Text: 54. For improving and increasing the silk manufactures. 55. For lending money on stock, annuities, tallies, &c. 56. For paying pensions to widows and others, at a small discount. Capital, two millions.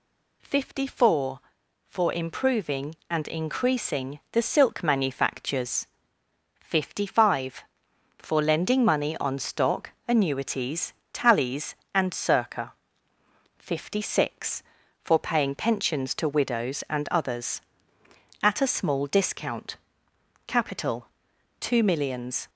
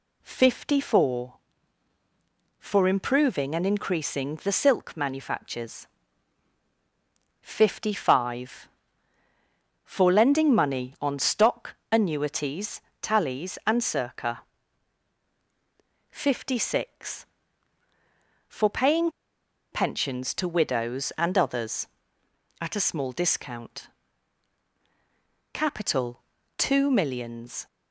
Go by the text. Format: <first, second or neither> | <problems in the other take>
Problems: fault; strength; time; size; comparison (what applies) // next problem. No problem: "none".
first | pauses between "paying" and "pensions"; noticeable; at 19.1 s; 0.62 s long